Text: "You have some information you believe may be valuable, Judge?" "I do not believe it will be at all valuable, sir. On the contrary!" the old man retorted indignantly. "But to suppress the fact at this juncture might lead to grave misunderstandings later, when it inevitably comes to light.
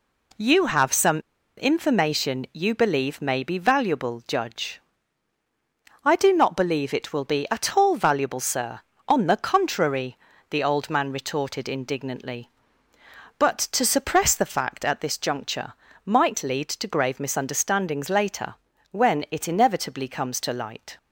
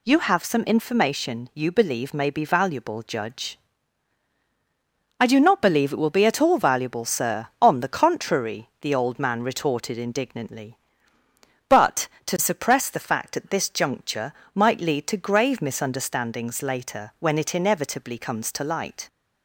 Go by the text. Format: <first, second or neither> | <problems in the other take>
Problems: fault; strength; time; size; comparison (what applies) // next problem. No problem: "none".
second | pauses between "some" and "information"; at 1.1 s; 0.39 s long // pauses between "juncture" and "might"; slight; at 15.7 s; 0.34 s long; slight in the second